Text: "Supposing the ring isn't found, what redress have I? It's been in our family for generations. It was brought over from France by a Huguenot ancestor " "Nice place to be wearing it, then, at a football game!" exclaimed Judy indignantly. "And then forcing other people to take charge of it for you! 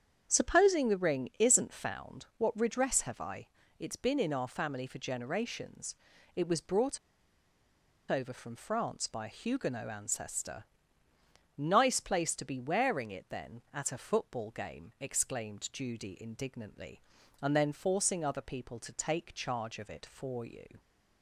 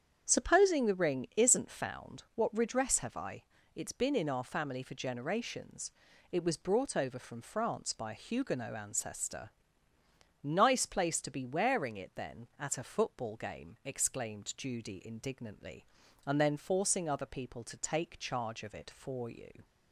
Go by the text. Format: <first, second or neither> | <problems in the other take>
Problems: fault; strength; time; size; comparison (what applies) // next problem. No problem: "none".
second | starts louder than the rest; strong; until 1.3 s; 8 dB; strong in the second // pauses between "brought" and "over"; at 6.9 s; 1.1 s long